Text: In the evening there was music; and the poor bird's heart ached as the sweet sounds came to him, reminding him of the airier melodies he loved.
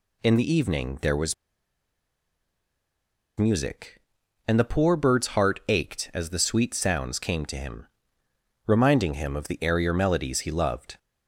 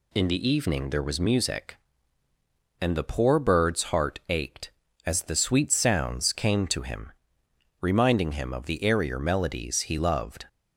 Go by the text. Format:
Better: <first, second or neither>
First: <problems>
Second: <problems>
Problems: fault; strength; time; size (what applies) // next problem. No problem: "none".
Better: second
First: pauses between "was" and "music"; strong; at 1.3 s; 2.0 s long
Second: none